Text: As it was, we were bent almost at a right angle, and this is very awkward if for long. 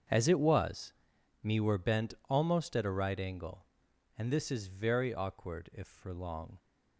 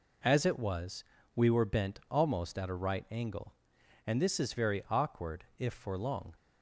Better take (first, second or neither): second